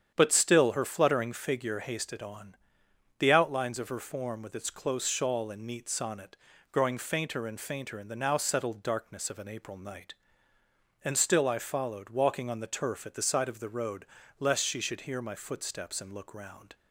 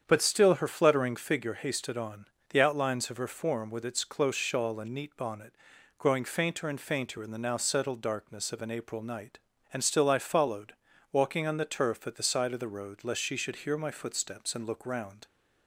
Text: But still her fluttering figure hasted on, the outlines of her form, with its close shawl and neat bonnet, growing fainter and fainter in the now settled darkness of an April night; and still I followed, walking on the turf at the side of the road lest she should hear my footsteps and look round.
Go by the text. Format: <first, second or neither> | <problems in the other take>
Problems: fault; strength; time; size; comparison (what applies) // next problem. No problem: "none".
second | starts louder than the rest; strong; until 1.1 s; 8.5 dB; strong in the second // says "sonnet" for "bonnet"; at 5.8 s // pauses between "road" and "lest"; slight; at 14.0 s; 0.34 s long